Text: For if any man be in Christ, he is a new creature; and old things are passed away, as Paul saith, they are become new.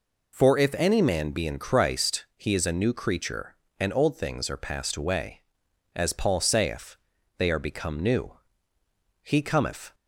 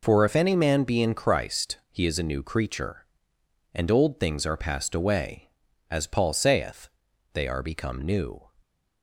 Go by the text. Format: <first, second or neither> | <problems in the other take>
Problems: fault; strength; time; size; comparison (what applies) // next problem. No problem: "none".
second | goes on to say "He cometh"; noticeable; from 9.2 s on; 0.72 s long